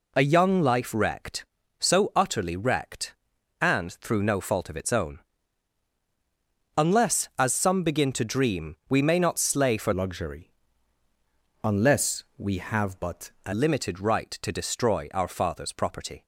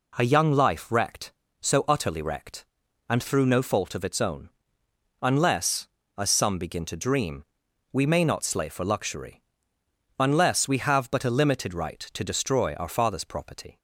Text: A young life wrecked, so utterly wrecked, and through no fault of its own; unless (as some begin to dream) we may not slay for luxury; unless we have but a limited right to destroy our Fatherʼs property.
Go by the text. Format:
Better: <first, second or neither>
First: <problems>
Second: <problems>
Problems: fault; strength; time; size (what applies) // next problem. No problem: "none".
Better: second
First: changes voice from "luxury" to "a"; from 9.9 to 13.5 s; 3.6 s long // pauses between "unless" and "we"; slight; at 12.2 s; 0.16 s long // pauses between "but" and "a"; slight; at 13.2 s; 0.16 s long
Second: none